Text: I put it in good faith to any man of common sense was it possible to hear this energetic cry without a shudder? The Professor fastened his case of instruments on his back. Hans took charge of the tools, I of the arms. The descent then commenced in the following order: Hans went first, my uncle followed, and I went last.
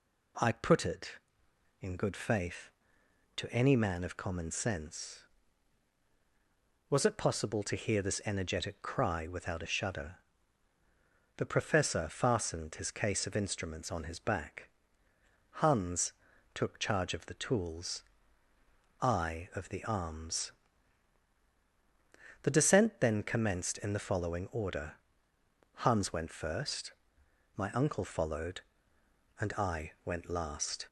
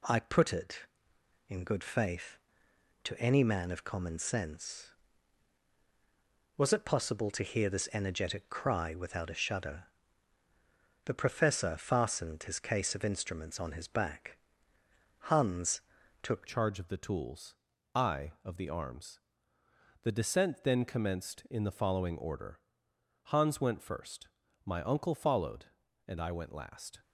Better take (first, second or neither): first